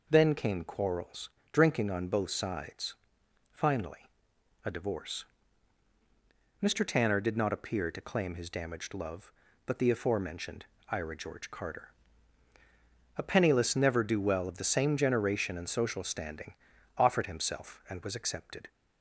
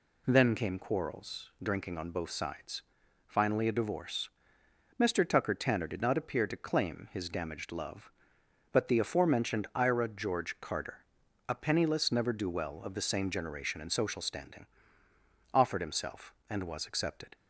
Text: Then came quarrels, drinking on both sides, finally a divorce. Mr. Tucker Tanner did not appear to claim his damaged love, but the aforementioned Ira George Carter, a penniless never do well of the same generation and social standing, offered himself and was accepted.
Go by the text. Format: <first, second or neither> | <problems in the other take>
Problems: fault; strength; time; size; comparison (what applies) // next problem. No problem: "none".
second | pauses between "finally" and "a"; noticeable; at 4.0 s; 0.58 s long // skips "Tucker"; at 6.8 s // pauses between "aforementioned" and "Ira"; slight; at 10.6 s; 0.26 s long